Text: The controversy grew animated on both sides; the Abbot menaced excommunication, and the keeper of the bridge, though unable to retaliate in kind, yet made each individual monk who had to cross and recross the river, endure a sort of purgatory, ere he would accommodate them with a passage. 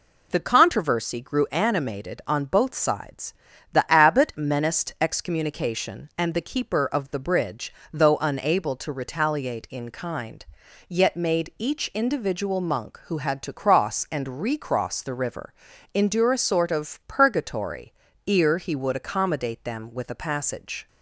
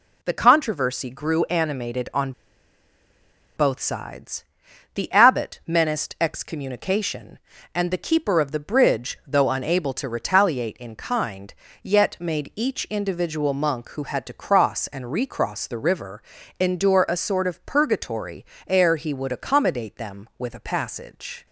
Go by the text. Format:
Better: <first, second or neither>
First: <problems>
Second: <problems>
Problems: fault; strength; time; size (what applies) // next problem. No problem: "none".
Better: first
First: none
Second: pauses between "on" and "both"; strong; at 2.3 s; 1.2 s long